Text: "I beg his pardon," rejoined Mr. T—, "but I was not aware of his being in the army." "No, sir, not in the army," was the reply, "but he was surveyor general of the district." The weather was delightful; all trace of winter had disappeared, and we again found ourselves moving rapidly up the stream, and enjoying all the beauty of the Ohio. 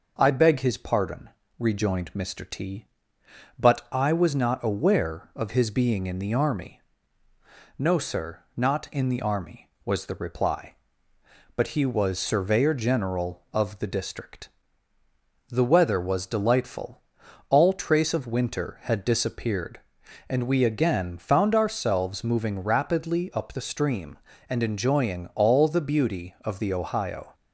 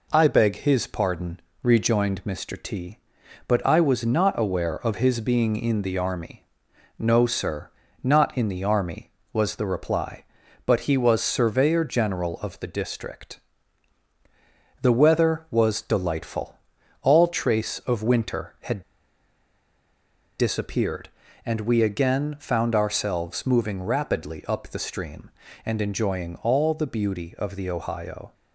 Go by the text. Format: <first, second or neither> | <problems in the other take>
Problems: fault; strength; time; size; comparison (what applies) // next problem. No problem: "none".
first | pauses between "had" and "disappeared"; strong; at 18.8 s; 1.5 s long